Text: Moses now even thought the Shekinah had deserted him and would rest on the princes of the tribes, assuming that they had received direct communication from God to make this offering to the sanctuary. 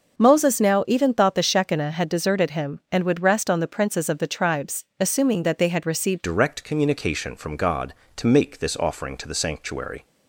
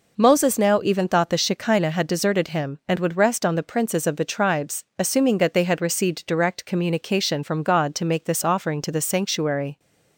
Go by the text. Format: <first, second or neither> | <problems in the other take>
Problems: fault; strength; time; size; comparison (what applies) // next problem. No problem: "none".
second | starts louder than the rest; until 1.2 s; 6.5 dB // changes voice at "direct"; from 6.2 s on; 3.8 s long